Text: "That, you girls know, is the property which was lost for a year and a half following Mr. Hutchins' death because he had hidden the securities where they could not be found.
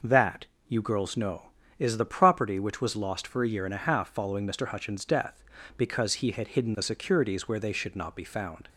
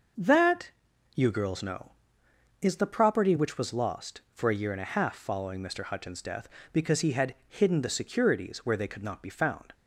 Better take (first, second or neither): second